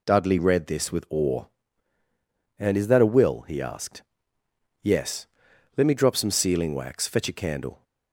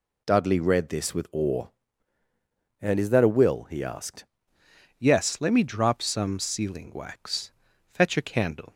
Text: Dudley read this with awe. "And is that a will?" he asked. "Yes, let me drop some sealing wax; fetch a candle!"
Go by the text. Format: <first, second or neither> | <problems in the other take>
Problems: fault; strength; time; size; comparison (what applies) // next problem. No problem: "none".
first | changes voice at "Yes"; from 4.9 s on; 3.8 s long